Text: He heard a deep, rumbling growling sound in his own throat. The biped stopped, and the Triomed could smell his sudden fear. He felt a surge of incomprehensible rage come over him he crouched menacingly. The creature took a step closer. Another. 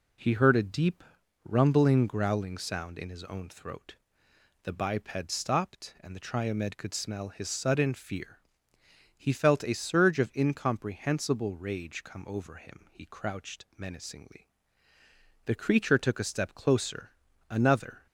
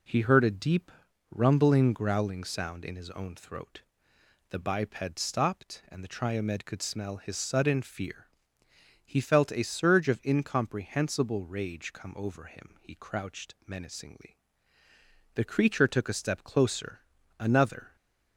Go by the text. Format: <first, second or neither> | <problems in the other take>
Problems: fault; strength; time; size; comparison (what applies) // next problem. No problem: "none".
neither | none